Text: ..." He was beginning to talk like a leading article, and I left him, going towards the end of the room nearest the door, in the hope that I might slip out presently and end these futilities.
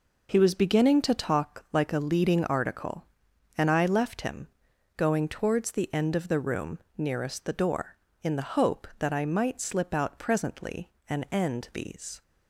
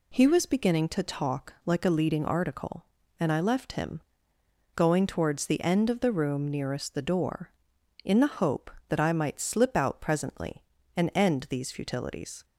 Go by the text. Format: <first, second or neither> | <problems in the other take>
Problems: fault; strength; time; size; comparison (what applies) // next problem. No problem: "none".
second | pauses between "room" and "nearest"; slight; at 6.7 s; 0.18 s long // stops before "futilities"; at 12.2 s